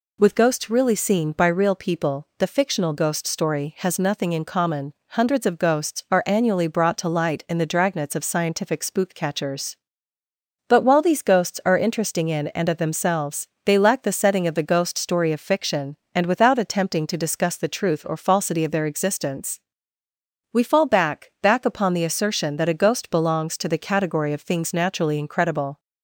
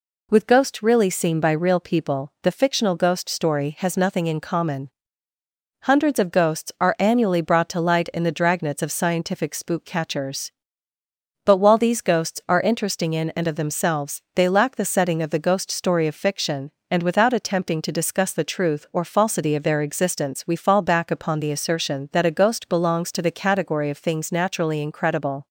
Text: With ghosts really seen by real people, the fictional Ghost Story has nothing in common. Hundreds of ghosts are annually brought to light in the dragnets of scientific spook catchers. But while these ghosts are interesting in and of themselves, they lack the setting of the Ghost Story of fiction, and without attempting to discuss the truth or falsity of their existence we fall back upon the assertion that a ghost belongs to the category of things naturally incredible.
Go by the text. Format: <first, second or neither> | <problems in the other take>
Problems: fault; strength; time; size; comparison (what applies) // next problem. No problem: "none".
second | pauses between "existence" and "we"; noticeable; at 19.6 s; 0.90 s long // says "back" twice; at 21.4 s